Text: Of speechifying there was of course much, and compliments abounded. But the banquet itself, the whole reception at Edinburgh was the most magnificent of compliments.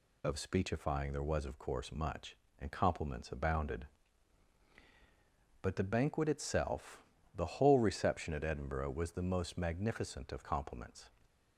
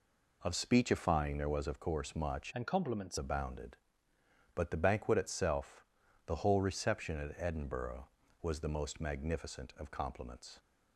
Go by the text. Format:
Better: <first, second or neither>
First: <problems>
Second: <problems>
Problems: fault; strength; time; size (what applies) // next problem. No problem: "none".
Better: first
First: none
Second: changes voice from "and" to "compliments"; from 2.5 to 3.1 s; 0.6 s long